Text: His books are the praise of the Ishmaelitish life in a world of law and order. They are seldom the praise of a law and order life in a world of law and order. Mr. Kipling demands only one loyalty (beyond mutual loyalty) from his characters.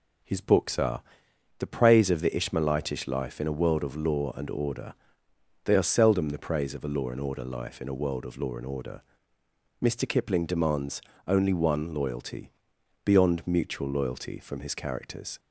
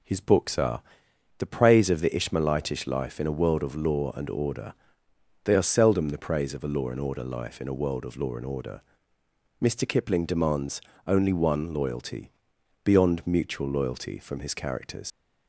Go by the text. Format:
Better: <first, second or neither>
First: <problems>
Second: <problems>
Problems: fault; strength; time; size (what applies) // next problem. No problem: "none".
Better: first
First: pauses between "are" and "the"; noticeable; at 1.0 s; 0.58 s long // pauses between "demands" and "only"; slight; at 11.0 s; 0.26 s long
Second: pauses between "are" and "the"; noticeable; at 0.8 s; 0.58 s long // pauses between "demands" and "only"; slight; at 10.8 s; 0.26 s long // leaves "characters" unfinished; at 15.1 s; 85 ms